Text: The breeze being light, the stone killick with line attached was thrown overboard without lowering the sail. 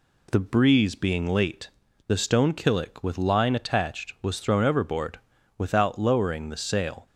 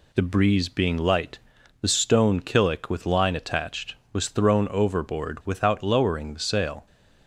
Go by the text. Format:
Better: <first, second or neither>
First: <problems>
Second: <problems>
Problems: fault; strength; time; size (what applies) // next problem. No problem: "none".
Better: second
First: says "late" for "light"; at 1.2 s // pauses between "overboard" and "without"; at 5.1 s; 0.38 s long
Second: none